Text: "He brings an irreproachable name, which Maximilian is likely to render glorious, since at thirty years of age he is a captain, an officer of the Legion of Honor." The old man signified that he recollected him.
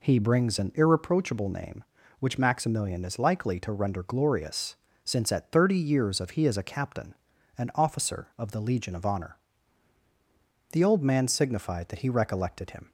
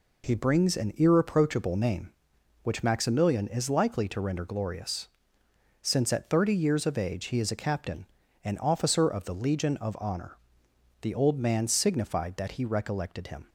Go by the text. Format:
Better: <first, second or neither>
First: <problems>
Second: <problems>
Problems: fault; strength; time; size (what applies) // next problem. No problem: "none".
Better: second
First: skips "age"; at 6.3 s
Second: none